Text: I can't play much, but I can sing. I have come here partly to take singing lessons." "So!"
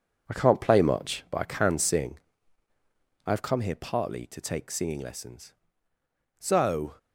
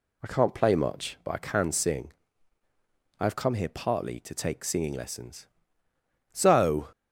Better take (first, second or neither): second